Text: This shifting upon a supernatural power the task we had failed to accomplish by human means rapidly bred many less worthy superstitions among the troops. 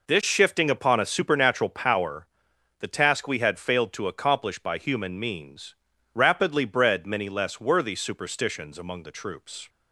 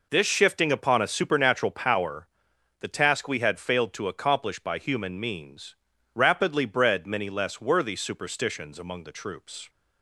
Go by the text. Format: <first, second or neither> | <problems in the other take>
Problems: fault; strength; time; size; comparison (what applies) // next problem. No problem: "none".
neither | pauses between "power" and "the"; noticeable; the same in both // pauses between "means" and "rapidly"; the same in both